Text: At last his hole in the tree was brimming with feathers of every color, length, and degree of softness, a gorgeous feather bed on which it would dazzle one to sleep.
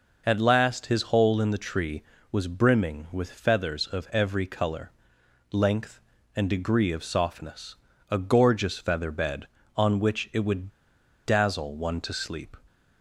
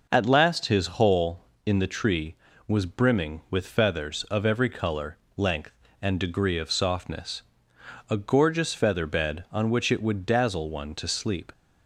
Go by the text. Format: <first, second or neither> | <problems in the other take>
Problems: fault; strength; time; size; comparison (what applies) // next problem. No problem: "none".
second | pauses between "would" and "dazzle"; noticeable; at 10.7 s; 0.54 s long